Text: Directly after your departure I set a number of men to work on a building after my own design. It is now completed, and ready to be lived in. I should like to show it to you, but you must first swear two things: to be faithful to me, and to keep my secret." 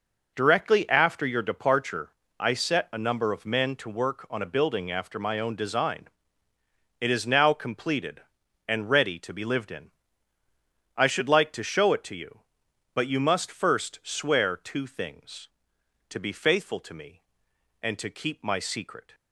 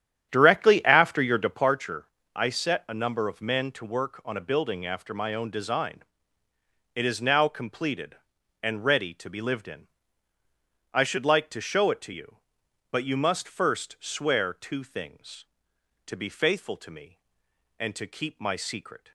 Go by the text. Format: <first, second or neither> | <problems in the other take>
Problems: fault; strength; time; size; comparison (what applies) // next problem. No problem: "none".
first | starts louder than the rest; strong; until 1.7 s; 10 dB // pauses between "departure" and "I"; slight; at 2.0 s; 0.30 s long; slight in the first